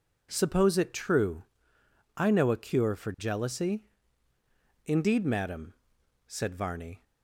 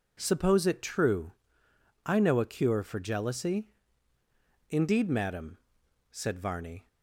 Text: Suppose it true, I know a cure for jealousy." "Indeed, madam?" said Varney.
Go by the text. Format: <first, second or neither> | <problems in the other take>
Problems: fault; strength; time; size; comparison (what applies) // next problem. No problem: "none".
neither | none